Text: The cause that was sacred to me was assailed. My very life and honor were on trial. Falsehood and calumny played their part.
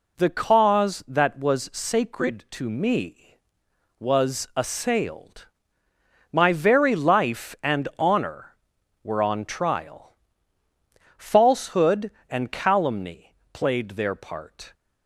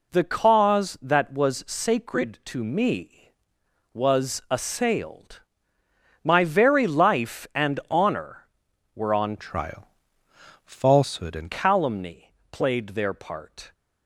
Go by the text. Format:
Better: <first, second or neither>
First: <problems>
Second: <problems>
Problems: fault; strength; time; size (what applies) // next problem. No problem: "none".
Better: first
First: pauses between "calumny" and "played"; slight; at 13.3 s; 0.16 s long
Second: changes voice from "trial" to "and"; from 9.3 to 11.5 s; 2.2 s long // pauses between "calumny" and "played"; slight; at 12.3 s; 0.16 s long